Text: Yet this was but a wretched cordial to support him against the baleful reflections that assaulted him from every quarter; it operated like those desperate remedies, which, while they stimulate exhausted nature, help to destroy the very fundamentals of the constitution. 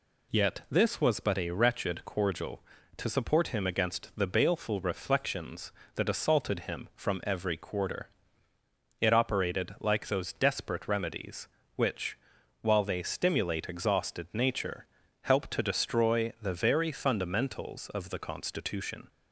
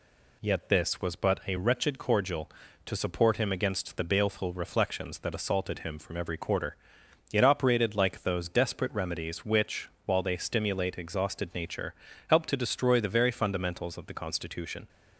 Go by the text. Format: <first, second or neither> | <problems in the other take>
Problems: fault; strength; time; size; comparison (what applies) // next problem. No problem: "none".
neither | none